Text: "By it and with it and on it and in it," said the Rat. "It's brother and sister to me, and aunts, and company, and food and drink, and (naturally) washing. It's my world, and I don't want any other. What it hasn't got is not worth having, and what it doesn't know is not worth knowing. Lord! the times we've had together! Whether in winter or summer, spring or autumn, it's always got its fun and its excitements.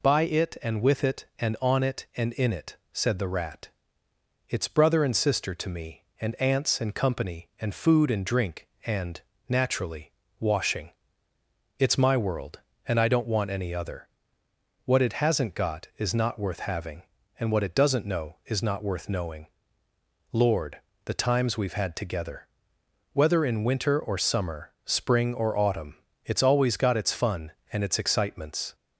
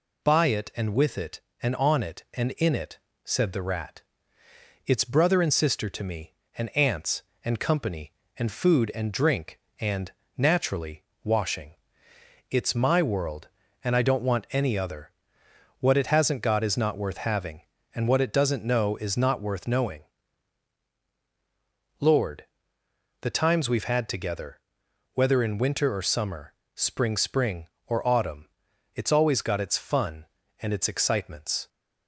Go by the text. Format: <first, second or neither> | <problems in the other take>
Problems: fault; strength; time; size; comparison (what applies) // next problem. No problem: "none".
first | says "spring" twice; at 27.1 s